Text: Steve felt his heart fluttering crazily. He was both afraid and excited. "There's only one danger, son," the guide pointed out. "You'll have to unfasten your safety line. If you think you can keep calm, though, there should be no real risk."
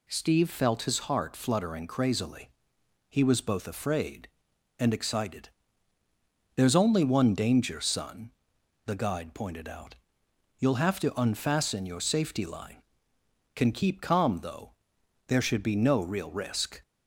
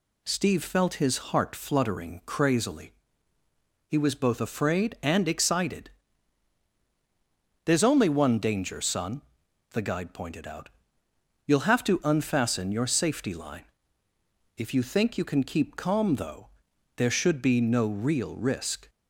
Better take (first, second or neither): second